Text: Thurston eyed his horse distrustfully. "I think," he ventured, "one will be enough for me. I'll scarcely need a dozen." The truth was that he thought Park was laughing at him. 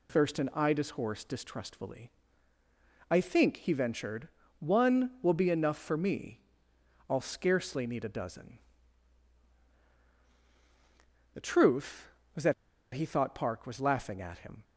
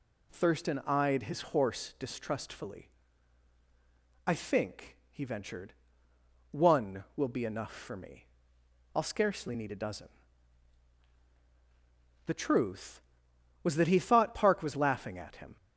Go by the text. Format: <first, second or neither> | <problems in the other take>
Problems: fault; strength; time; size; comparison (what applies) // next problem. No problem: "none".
second | pauses between "that" and "he"; at 12.5 s; 0.41 s long